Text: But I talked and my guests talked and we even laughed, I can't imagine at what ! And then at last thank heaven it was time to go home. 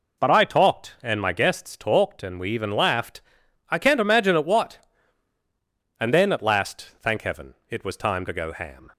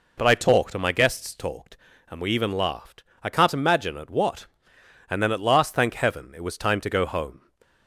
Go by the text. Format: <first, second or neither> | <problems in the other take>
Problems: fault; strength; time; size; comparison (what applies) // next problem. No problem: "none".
second | pauses between "heaven" and "it"; slight; at 7.5 s; 0.16 s long // says "ham" for "home"; at 8.5 s